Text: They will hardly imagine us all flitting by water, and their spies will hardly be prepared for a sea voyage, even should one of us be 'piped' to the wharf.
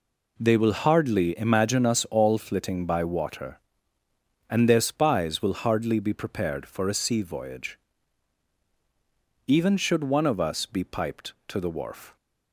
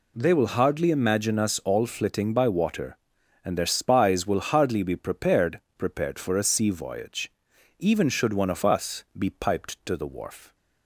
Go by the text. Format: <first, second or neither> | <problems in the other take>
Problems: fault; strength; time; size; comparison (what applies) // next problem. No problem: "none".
first | says "prepared" twice; at 5.7 s // pauses between "us" and "be"; slight; at 9.0 s; 0.16 s long